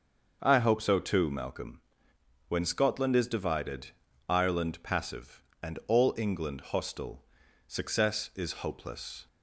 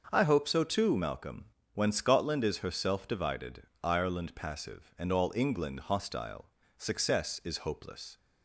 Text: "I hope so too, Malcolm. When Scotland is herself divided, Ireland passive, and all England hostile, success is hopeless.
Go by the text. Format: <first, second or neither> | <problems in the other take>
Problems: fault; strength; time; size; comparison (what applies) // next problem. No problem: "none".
second | starts louder than the rest; noticeable; until 1.4 s; 6 dB; also in the second // skips "herself"; at 3.2 s